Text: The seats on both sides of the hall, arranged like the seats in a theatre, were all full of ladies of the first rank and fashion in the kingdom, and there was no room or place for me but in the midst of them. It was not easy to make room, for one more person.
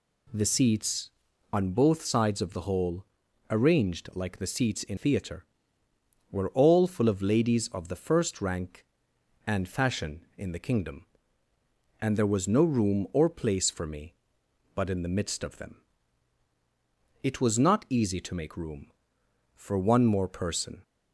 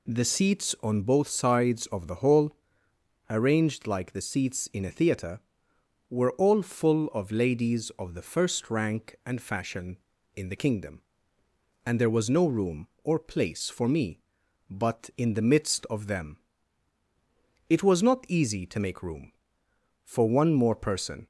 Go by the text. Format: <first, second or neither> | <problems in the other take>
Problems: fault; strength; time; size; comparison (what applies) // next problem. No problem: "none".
second | skips "a"; at 4.9 s